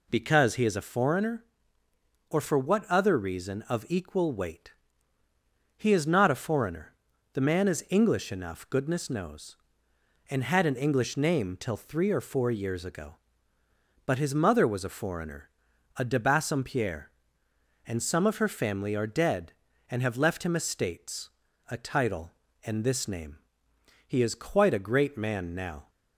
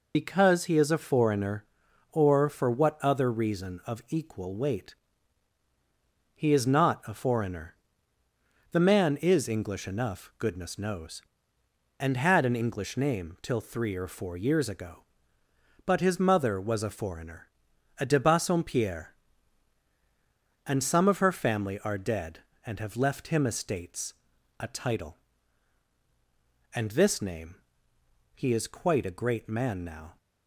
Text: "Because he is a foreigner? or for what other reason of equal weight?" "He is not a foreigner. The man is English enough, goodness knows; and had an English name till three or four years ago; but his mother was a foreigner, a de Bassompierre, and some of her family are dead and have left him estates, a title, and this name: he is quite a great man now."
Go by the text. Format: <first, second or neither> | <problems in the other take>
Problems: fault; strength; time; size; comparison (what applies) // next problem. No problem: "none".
first | loses the start of "Because"; at 0.1 s; 60 ms